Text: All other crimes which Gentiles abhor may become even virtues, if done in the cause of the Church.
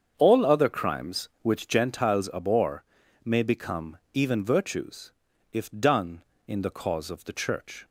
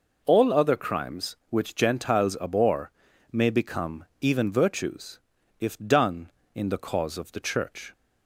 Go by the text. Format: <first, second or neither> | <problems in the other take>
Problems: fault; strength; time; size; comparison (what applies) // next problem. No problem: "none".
second | starts louder than the rest; strong; until 1.9 s; 7.5 dB // pauses between "abhor" and "may"; at 2.8 s; 0.40 s long; also in the second // pauses between "become" and "even"; slight; at 3.9 s; 0.16 s long; slight in the second